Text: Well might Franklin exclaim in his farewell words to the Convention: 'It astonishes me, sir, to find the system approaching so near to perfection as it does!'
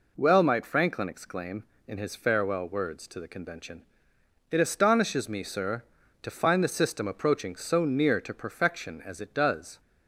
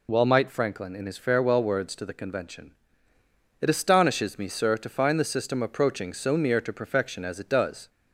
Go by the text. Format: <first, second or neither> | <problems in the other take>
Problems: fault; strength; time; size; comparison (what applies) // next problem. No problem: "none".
first | skips "exclaim"; at 0.9 s